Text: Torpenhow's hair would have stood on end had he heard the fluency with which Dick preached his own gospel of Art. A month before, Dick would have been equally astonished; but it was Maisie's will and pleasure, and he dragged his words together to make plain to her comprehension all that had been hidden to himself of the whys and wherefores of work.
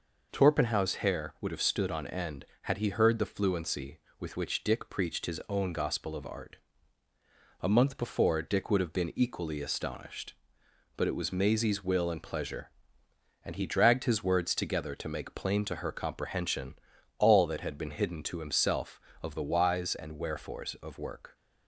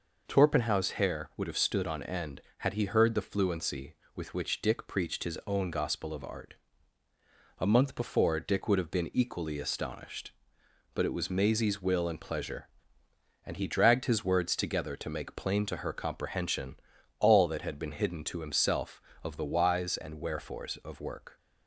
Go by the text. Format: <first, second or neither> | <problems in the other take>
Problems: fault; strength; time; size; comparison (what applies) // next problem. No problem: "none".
neither | pauses between "comprehension" and "all"; the same in both